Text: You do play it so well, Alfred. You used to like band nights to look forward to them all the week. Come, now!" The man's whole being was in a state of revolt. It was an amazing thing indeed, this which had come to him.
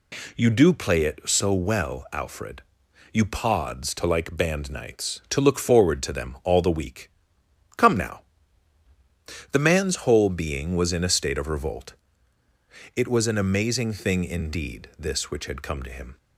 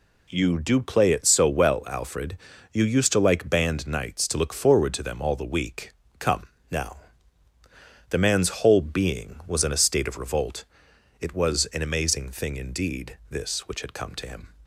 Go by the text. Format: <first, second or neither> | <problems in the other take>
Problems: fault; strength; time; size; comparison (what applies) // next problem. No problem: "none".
second | says "pods" for "used"; at 3.2 s